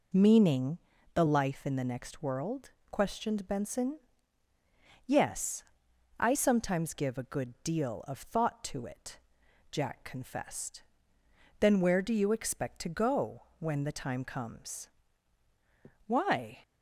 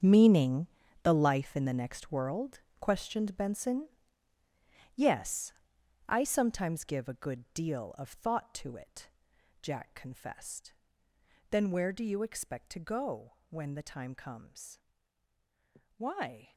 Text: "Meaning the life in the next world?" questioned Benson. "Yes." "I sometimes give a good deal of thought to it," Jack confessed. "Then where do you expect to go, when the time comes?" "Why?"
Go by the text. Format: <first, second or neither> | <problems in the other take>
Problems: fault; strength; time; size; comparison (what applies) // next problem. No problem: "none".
first | gets quieter; strong; throughout; 14 dB // pauses between "Meaning" and "the"; at 0.6 s; 0.38 s long; also in the first